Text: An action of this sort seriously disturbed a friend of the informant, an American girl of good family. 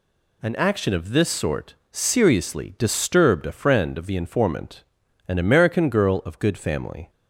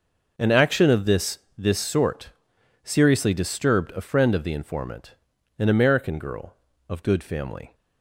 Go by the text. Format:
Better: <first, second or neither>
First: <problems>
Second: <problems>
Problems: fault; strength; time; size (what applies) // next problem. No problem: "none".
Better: first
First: pauses between "sort" and "seriously"; slight; at 1.7 s; 0.18 s long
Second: says "this" twice; at 1.5 s // pauses between "sort" and "seriously"; noticeable; at 2.3 s; 0.52 s long